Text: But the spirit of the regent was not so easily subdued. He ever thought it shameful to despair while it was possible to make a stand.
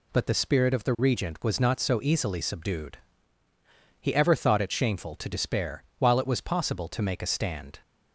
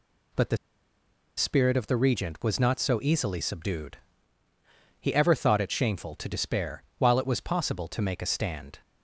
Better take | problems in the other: first | pauses between "the" and "spirit"; noticeable; at 0.5 s; 0.80 s long // pauses between "despair" and "while"; slight; at 6.8 s; 0.16 s long; slight in the first

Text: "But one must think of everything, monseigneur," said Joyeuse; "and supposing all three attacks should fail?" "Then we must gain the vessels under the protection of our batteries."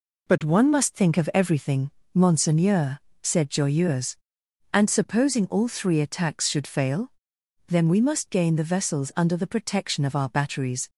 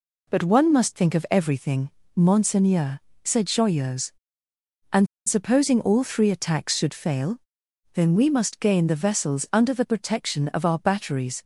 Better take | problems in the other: first | pauses between "and" and "supposing"; slight; at 5.0 s; 0.20 s long

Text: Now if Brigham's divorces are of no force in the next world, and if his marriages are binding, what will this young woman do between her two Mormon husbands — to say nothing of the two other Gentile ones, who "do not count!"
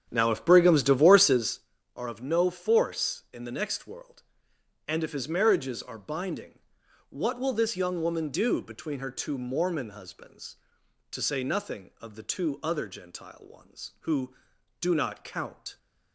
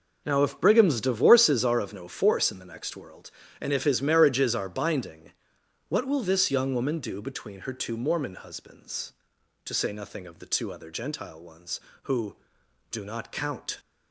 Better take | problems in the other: second | starts louder than the rest; strong; until 1.6 s; 8.5 dB

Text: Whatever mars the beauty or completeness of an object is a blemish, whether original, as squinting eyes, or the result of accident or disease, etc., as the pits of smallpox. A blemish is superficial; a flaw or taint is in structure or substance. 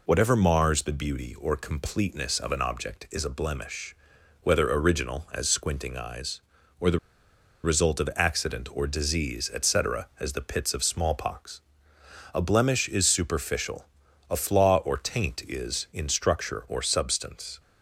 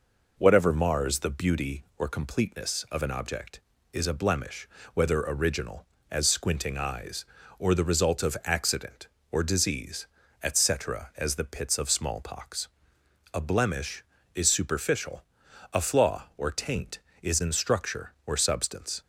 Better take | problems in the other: second | pauses between "the" and "result"; noticeable; at 6.9 s; 0.65 s long

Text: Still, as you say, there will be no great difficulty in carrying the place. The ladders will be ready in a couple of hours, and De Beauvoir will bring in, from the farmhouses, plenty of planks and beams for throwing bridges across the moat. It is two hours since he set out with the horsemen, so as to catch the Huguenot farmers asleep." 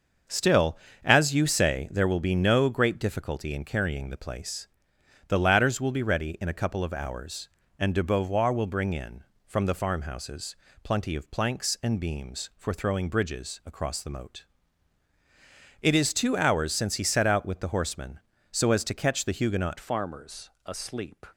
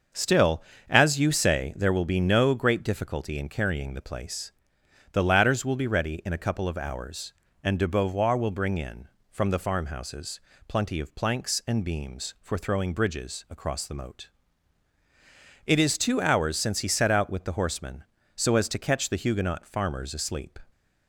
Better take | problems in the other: second | starts louder than the rest; until 1.5 s; 6.5 dB; also in the second // changes voice at "farmers"; from 19.7 s on; 1.5 s long // pauses between "farmers" and "asleep"; slight; at 20.4 s; 0.16 s long

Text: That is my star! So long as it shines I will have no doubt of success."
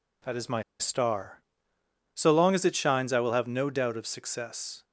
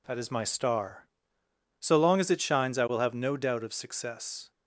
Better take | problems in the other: second | pauses between "my" and "star"; slight; at 0.6 s; 0.18 s long

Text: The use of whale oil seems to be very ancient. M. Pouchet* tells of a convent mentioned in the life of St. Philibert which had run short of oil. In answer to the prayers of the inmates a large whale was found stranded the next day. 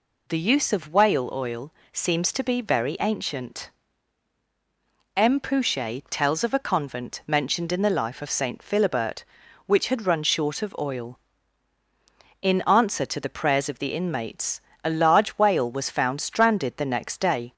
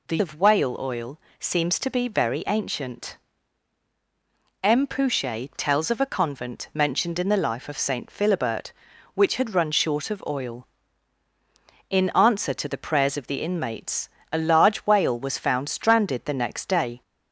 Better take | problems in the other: first | skips "use"; at 0.1 s // pauses between "oil" and "seems"; slight; at 1.1 s; 0.18 s long; slight in the first // pauses between "inmates" and "a"; slight; at 14.0 s; 0.22 s long; slight in the first

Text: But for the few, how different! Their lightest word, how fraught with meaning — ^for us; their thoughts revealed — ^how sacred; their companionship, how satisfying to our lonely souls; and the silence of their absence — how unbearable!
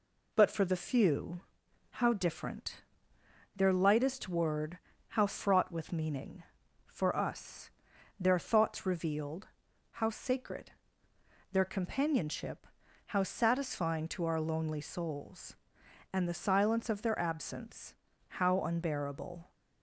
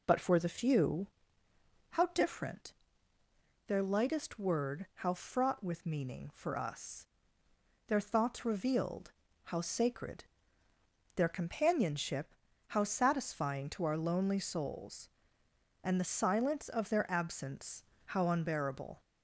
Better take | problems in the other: neither | none

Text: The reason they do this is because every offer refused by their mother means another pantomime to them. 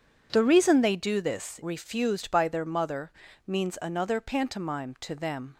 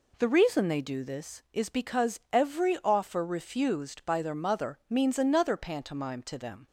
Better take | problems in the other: second | skips "is because every offer"; at 1.6 s // pauses between "mother" and "means"; slight; at 3.1 s; 0.34 s long

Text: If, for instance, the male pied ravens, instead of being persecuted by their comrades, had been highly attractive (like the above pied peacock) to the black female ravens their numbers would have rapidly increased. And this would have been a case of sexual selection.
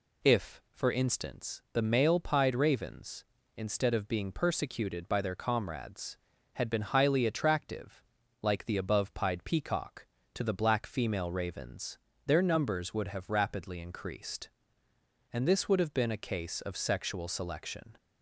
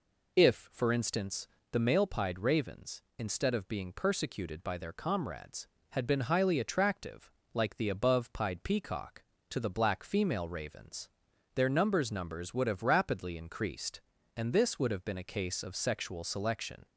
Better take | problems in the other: first | pauses between "ravens" and "their"; noticeable; at 11.0 s; 0.46 s long; slight in the first // says "numbers" twice; at 12.0 s

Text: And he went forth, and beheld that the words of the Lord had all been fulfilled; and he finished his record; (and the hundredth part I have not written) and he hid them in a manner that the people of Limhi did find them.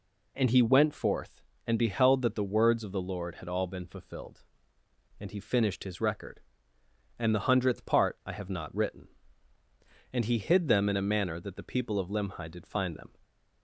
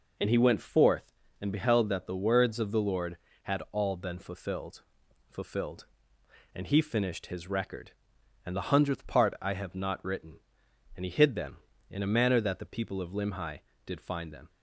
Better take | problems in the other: first | says "fulfilled" twice; at 5.3 s

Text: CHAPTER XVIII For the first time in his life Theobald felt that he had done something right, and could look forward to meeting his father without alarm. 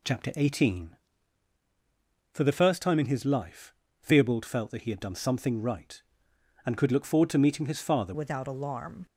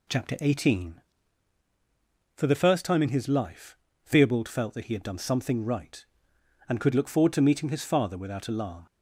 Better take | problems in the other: second | pauses between "life" and "Theobald"; slight; at 3.7 s; 0.30 s long; slight in the second // changes voice at "without"; from 8.1 s on; 0.9 s long

